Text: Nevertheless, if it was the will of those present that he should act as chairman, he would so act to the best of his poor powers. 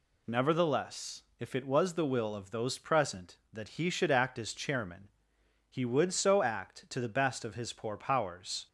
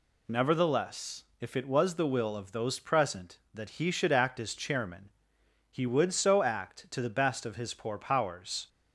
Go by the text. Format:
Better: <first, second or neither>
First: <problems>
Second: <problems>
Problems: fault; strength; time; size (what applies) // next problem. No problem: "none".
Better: neither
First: none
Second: none